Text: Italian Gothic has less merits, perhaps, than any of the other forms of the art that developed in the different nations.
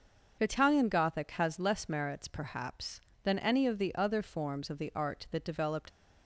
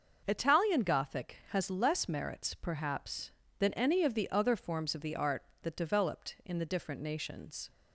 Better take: second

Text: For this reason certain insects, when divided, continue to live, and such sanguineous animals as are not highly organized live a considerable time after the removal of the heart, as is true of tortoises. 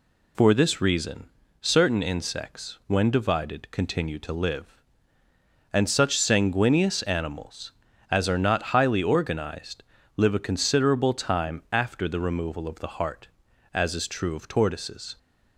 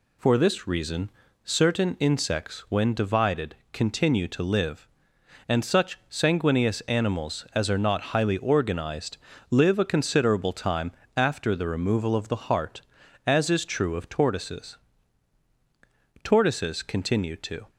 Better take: first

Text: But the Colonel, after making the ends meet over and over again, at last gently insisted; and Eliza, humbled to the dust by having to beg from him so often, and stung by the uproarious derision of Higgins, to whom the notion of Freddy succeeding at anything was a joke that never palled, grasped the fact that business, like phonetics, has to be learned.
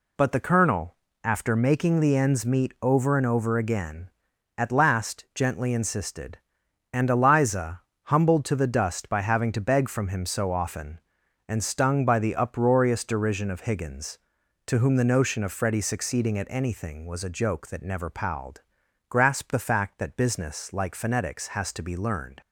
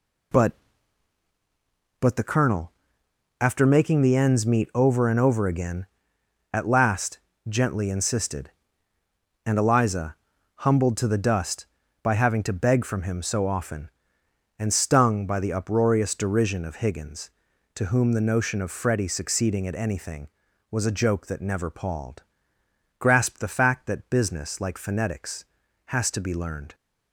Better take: first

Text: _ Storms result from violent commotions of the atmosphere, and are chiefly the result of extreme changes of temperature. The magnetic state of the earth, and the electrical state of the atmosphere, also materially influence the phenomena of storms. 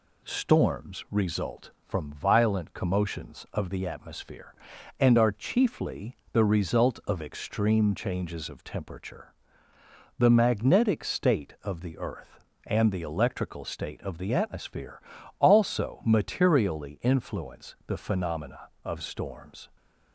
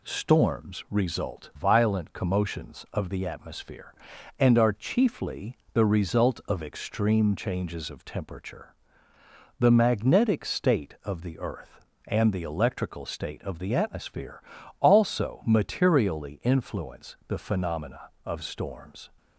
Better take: first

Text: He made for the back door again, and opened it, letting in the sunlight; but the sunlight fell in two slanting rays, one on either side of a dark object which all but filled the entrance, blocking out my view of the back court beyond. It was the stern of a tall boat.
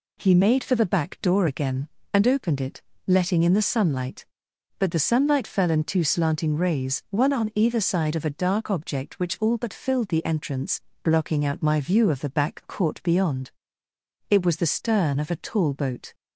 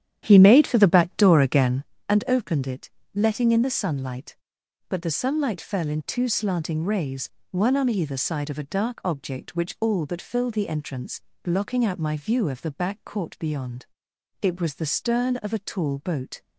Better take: first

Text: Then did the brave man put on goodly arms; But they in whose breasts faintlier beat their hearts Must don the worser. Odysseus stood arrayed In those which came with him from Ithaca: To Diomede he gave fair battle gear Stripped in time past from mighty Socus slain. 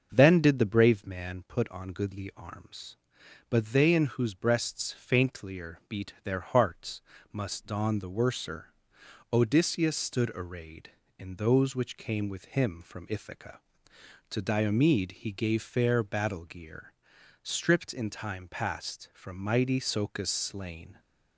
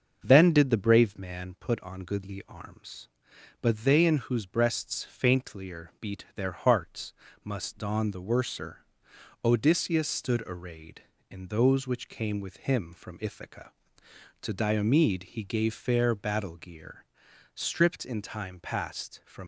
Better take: first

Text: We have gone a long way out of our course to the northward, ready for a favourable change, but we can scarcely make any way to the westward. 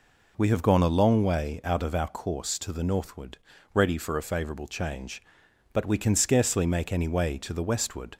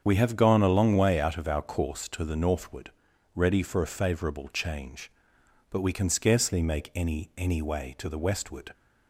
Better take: first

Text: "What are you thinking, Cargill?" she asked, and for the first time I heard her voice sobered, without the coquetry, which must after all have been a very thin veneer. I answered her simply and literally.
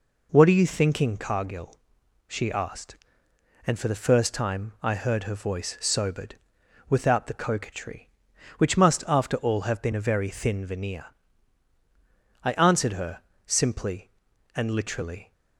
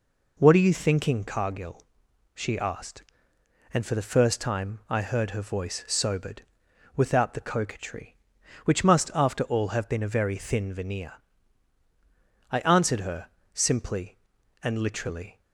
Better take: neither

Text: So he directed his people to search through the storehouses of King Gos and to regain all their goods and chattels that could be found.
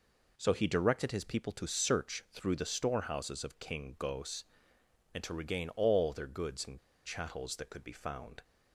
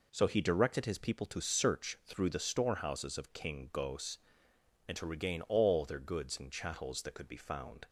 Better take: second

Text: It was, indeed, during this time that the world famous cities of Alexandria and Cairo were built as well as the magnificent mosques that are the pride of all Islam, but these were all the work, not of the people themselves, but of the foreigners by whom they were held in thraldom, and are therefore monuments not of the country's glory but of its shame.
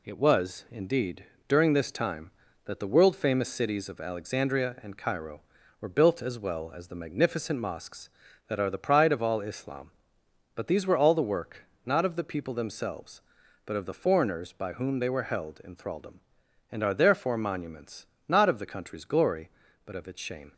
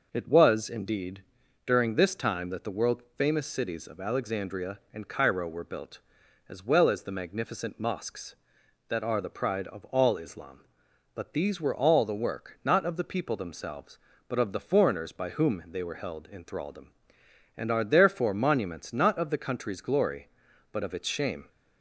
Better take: second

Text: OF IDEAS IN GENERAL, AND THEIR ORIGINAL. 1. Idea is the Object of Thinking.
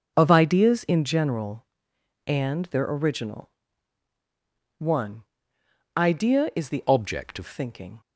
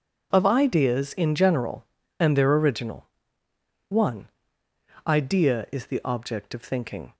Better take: second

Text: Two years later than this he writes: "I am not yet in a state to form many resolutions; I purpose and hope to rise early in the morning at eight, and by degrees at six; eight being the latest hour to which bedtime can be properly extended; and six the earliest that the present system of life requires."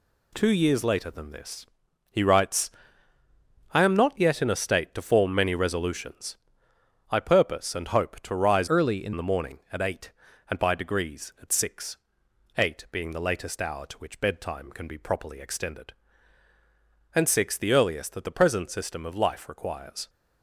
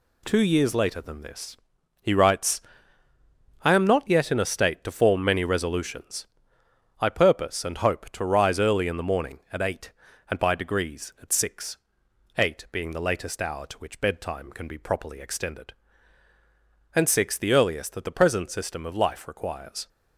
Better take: second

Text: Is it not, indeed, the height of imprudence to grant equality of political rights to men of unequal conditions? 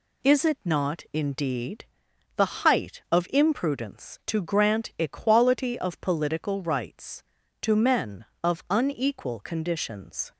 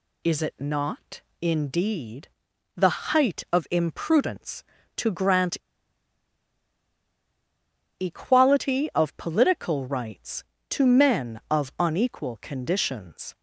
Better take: first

